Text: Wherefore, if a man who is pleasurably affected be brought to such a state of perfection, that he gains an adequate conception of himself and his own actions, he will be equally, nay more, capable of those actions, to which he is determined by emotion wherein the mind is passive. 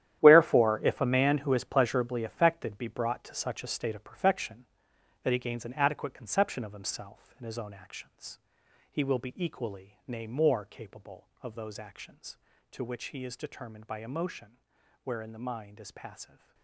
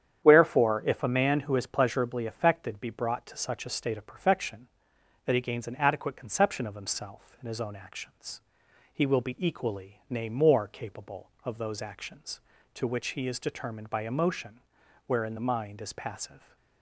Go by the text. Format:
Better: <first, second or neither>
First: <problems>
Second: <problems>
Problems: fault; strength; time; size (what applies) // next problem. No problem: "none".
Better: second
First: gets quieter; strong; throughout; 13.5 dB // starts louder than the rest; strong; until 1.2 s; 11.5 dB // pauses between "emotion" and "wherein"; noticeable; at 14.5 s; 0.48 s long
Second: starts louder than the rest; strong; until 1.2 s; 9 dB // pauses between "emotion" and "wherein"; noticeable; at 14.5 s; 0.48 s long